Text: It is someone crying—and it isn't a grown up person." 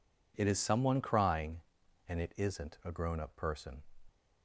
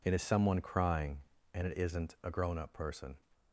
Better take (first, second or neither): neither